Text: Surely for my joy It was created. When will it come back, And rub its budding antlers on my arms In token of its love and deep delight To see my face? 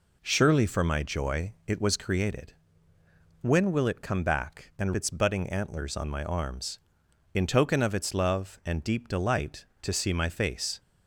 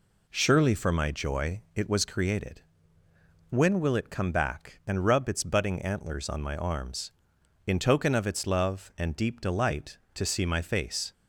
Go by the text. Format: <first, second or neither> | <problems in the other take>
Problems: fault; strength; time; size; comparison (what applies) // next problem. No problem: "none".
second | skips "rub"; at 4.9 s